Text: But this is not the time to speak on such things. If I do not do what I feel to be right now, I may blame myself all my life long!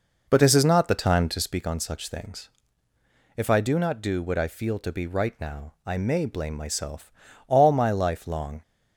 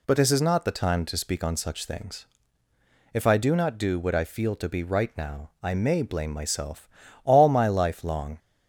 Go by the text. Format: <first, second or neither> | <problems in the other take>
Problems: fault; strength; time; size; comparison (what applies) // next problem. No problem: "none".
second | starts louder than the rest; noticeable; until 1.6 s; 5 dB // pauses between "myself" and "all"; slight; at 7.1 s; 0.36 s long; slight in the second